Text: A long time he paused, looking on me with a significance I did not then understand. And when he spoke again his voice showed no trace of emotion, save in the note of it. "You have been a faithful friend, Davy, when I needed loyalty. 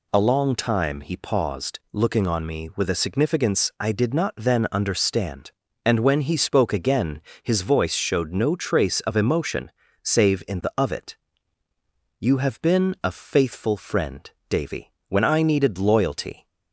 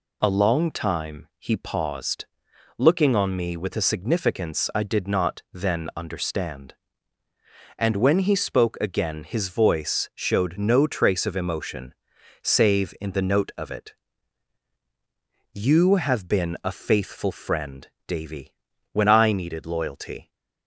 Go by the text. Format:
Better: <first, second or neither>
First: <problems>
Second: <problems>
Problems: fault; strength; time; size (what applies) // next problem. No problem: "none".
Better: second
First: pauses between "again" and "his"; slight; at 7.2 s; 0.22 s long // skips "note"; at 10.7 s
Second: none